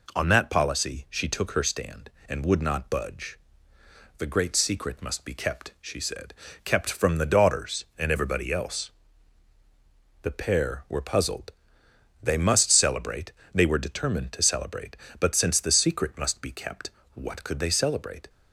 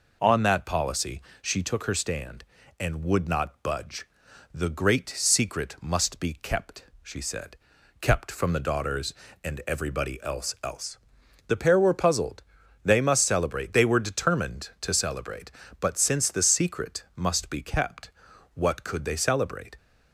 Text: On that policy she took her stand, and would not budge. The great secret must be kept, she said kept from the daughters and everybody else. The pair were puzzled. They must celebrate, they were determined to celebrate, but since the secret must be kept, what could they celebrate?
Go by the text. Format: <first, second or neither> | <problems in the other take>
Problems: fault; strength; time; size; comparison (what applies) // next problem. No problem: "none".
first | pauses between "policy" and "she"; slight; at 1.2 s; 0.20 s long // pauses between "said" and "kept"; at 7.5 s; 0.42 s long; slight in the first // says "else" twice; at 10.6 s